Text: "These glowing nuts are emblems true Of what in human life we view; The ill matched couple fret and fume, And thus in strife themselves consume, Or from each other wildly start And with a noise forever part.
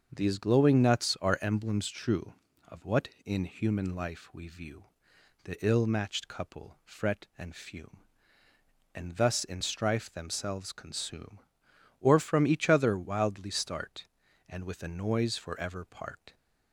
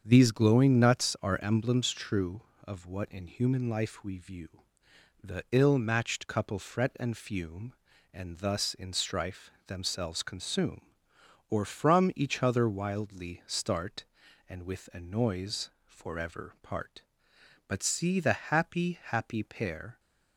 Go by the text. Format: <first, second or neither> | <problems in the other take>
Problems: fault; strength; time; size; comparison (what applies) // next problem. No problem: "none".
first | starts louder than the rest; strong; until 1.0 s; 7.5 dB; also in the first // pauses between "strife" and "themselves"; slight; at 9.5 s; 0.16 s long // pauses between "noise" and "forever"; slight; at 15.6 s; 0.16 s long // goes on to say "But see the happy happy pair"; strong; from 17.6 s on; 2.3 s long